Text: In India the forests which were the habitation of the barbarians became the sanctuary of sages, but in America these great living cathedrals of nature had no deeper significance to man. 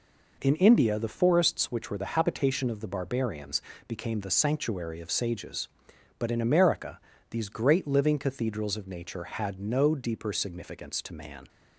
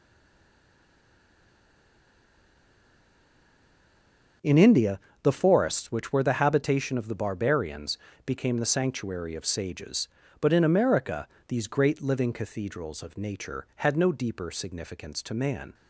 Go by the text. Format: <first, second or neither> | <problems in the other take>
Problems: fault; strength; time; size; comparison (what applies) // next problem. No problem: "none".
first | stays silent before the first word; strong; until 4.4 s; 4.4 s long // starts louder than the rest; until 5.6 s; 7 dB // pauses between "India" and "the"; slight; at 4.9 s; 0.22 s long // pauses between "barbarians" and "became"; slight; at 7.9 s; 0.26 s long; slight in the first // pauses between "America" and "these"; slight; at 11.2 s; 0.20 s long; slight in the first